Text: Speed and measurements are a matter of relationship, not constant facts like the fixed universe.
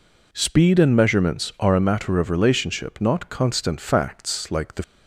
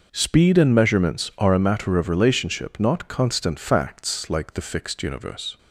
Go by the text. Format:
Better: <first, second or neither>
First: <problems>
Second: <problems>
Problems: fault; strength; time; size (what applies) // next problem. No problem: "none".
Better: second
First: stops before "fixed universe"; at 4.8 s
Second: none